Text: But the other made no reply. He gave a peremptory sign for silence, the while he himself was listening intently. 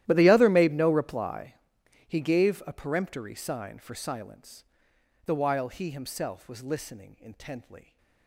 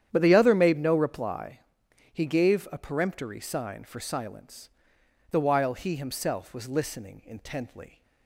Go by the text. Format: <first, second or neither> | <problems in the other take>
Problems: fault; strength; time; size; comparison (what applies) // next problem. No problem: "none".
second | gets quieter; strong; throughout; 21.5 dB // starts louder than the rest; strong; until 1.0 s; 13.5 dB; strong in the second